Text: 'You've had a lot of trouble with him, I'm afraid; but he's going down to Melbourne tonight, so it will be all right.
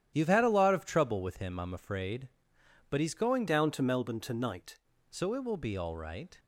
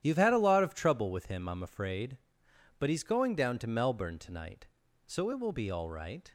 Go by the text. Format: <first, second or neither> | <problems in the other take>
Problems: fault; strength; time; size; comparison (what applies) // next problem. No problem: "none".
second | starts louder than the rest; strong; until 1.1 s; 10.5 dB; strong in the second // changes voice from "down" to "tonight"; from 3.4 to 4.7 s; 1.3 s long